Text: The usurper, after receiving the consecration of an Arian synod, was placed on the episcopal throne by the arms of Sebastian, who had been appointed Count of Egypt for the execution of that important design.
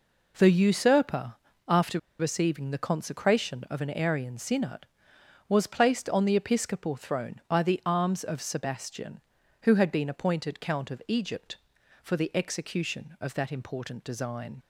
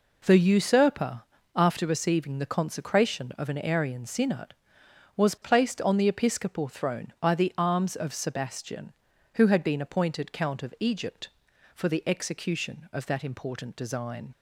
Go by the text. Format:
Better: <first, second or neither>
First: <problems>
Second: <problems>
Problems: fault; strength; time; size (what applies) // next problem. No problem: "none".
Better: second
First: pauses between "after" and "receiving"; slight; at 1.9 s; 0.21 s long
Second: none